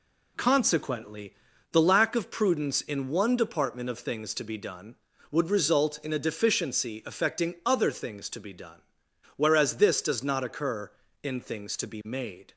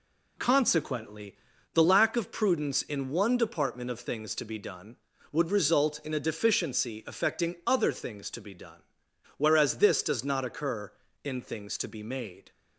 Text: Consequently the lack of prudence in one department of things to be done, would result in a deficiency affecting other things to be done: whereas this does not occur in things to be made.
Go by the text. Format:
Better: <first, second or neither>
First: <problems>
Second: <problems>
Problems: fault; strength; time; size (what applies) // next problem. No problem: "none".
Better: neither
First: pauses between "Consequently" and "the"; at 1.3 s; 0.38 s long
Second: pauses between "Consequently" and "the"; at 1.3 s; 0.38 s long